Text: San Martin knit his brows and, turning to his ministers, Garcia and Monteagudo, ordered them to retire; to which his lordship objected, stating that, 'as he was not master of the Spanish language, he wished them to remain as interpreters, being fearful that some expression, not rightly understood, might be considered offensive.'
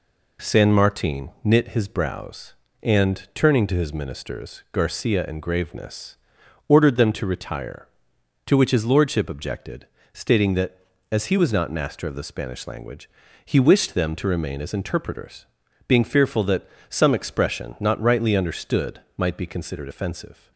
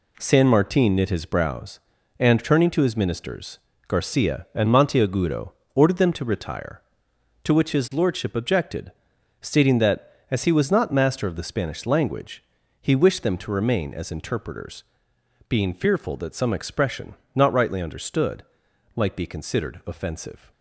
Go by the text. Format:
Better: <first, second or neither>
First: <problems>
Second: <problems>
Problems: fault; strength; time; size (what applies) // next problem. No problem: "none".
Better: second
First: pauses between "Martin" and "knit"; slight; at 1.2 s; 0.16 s long // says "Graveness" for "Monteagudo"; at 5.4 s // pauses between "that" and "some"; slight; at 16.6 s; 0.18 s long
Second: none